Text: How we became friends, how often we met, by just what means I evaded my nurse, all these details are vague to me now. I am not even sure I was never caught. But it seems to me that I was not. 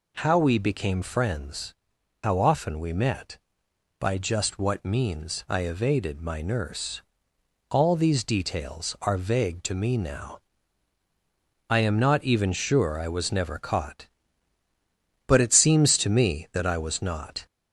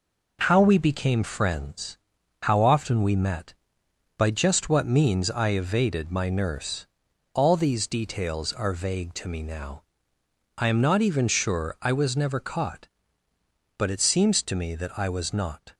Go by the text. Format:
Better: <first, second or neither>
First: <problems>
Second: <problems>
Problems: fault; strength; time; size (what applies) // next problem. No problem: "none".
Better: second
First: gets louder; slight; throughout; 2.5 dB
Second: none